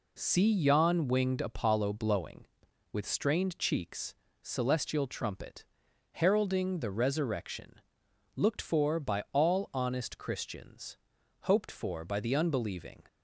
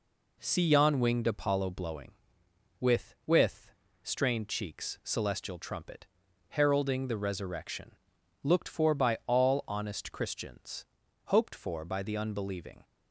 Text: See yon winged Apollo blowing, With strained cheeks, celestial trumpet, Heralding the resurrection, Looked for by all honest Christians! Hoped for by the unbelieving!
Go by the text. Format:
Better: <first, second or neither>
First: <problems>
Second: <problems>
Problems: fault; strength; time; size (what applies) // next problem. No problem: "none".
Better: first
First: none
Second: says "With" twice; at 3.2 s